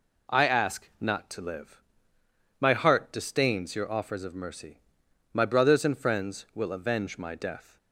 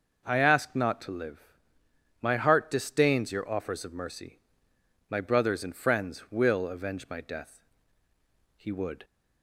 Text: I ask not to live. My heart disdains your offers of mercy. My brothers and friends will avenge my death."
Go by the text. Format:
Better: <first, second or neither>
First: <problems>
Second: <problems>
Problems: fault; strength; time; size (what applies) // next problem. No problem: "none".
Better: first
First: none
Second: goes on to say "He would"; slight; from 8.5 s on; 0.48 s long